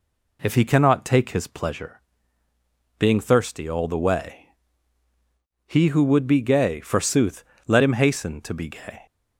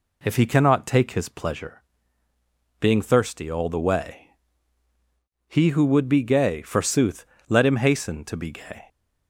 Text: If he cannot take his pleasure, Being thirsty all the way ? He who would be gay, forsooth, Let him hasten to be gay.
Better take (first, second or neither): neither